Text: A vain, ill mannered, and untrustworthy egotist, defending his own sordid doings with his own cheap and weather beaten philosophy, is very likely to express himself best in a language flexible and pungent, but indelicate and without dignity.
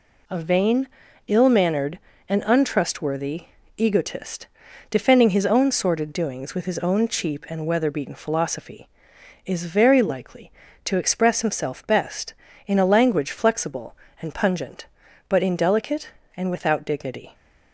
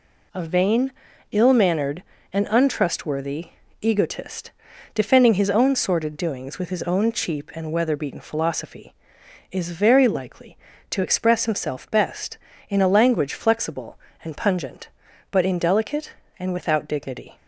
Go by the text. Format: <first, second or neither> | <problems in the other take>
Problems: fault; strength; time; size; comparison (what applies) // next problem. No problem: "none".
neither | pauses between "untrustworthy" and "egotist"; slight; the same in both